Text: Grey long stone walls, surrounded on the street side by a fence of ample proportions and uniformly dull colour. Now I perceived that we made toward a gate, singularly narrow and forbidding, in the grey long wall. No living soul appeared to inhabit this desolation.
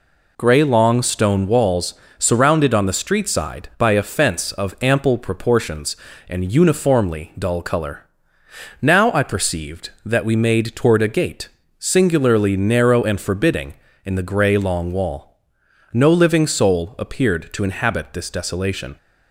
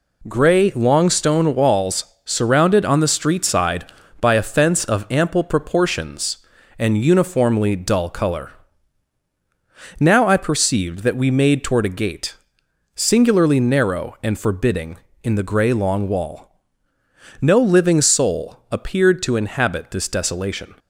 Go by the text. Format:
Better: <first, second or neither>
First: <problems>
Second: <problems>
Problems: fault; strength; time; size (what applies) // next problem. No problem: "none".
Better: neither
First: none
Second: none